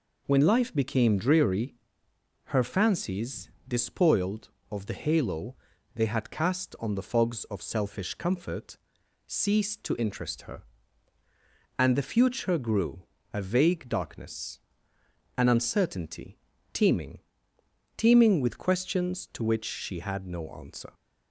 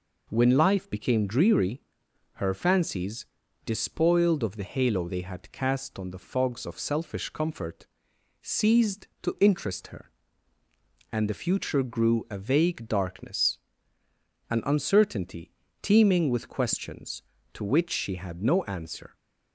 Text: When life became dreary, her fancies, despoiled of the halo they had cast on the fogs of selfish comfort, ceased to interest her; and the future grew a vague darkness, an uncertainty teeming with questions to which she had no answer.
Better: second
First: pauses between "halo" and "they"; at 5.5 s; 0.40 s long // pauses between "grew" and "a"; slight; at 13.0 s; 0.26 s long // pauses between "uncertainty" and "teeming"; slight; at 16.3 s; 0.34 s long // says "teeming" twice; at 17.9 s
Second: pauses between "uncertainty" and "teeming"; slight; at 15.5 s; 0.32 s long

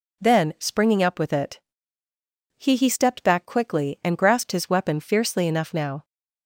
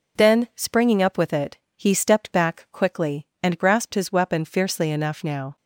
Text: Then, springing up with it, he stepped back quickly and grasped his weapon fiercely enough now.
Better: second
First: says "he" twice; at 2.7 s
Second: none

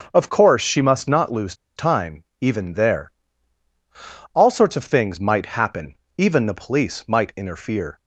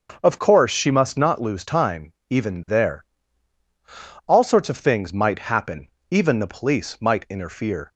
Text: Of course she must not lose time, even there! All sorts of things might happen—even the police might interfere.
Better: second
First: starts louder than the rest; until 1.1 s; 6 dB // pauses between "lose" and "time"; slight; at 1.5 s; 0.23 s long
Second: starts louder than the rest; until 1.2 s; 6 dB

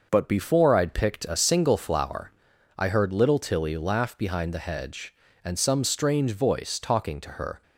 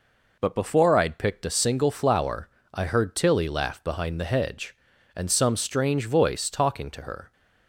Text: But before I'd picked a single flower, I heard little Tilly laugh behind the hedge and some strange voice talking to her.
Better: first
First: none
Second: skips "little"; at 3.1 s

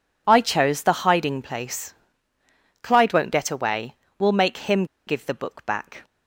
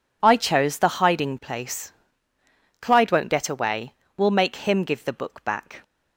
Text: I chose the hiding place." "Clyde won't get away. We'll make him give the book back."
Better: second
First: pauses between "him" and "give"; slight; at 4.8 s; 0.22 s long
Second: none

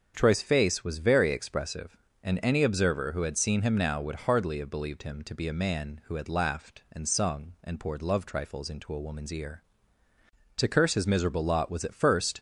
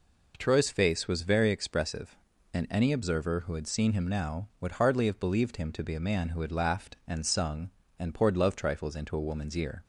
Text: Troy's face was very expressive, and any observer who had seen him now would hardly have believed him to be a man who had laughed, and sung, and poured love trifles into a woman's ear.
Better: second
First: starts louder than the rest; until 1.1 s; 6.5 dB // goes on to say "To curse his miserable lot was at first"; strong; from 10.5 s on; 1.8 s long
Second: none

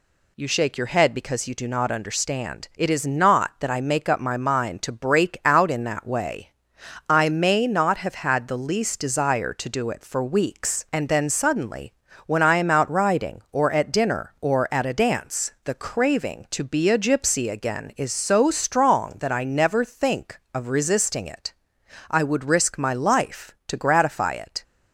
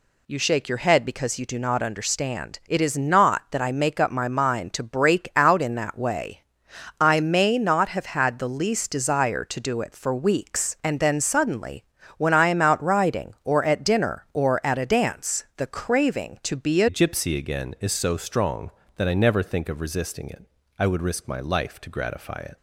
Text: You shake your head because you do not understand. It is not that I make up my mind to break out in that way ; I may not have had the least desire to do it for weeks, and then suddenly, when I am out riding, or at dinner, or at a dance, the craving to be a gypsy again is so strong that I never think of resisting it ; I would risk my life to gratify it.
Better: first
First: none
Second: changes voice at "gypsy"; from 16.8 s on; 5.7 s long

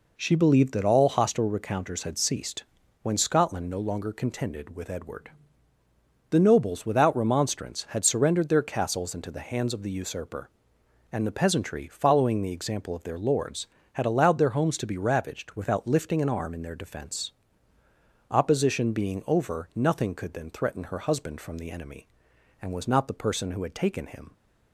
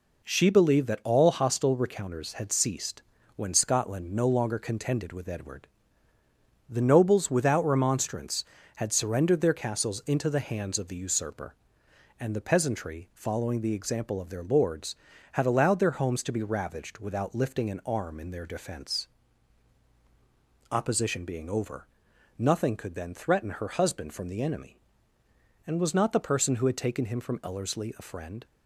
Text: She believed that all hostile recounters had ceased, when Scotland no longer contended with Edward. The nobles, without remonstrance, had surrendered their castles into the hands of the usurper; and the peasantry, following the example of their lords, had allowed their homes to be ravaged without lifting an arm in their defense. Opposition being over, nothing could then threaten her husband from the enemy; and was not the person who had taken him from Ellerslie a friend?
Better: second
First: stops before "from Ellerslie a friend"; at 24.3 s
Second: none

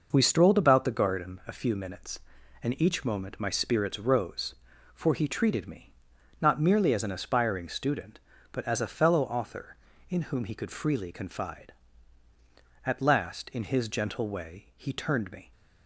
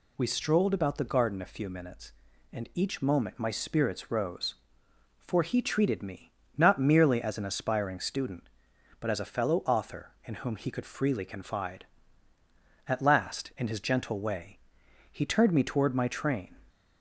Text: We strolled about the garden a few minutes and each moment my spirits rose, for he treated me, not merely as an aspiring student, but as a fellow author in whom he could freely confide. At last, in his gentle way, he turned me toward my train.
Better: second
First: stops before "toward my train"; at 15.5 s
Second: none

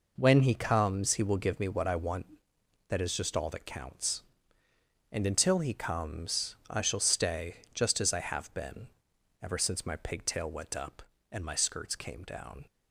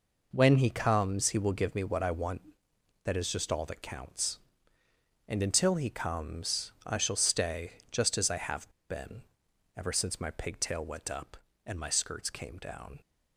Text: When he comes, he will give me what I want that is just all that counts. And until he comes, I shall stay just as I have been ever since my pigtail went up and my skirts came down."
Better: first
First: pauses between "stay" and "just"; slight; at 7.5 s; 0.18 s long // pauses between "been" and "ever"; noticeable; at 8.8 s; 0.56 s long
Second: pauses between "stay" and "just"; slight; at 7.7 s; 0.18 s long // pauses between "have" and "been"; slight; at 8.6 s; 0.19 s long // pauses between "been" and "ever"; noticeable; at 9.2 s; 0.56 s long

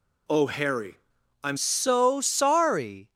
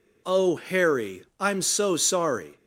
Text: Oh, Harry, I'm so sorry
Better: second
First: changes voice at "so"; from 1.5 s on; 1.6 s long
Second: none

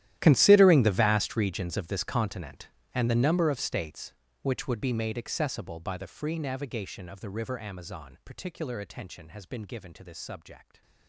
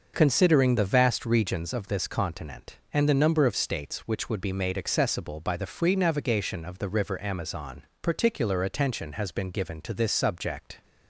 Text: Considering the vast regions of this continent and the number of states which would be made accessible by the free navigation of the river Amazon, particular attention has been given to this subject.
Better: second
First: gets quieter; strong; throughout; 19.5 dB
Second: none

